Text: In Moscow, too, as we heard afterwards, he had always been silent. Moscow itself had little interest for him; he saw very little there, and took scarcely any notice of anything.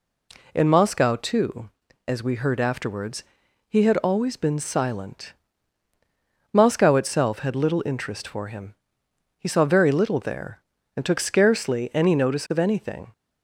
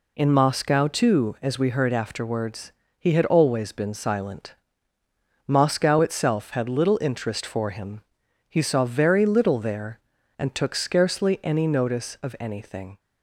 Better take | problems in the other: neither | none

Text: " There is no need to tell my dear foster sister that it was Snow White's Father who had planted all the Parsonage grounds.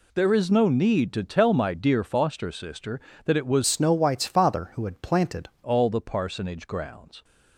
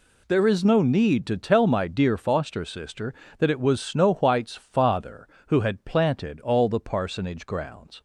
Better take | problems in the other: second | changes voice from "Snow" to "planted"; from 3.6 to 5.5 s; 1.9 s long

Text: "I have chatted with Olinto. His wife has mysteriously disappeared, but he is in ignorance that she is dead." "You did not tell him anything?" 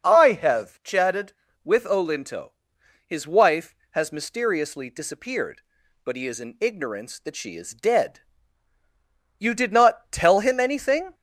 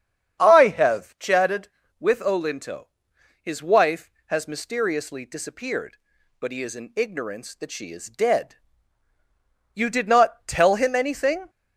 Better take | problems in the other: first | starts louder than the rest; strong; until 1.9 s; 8 dB

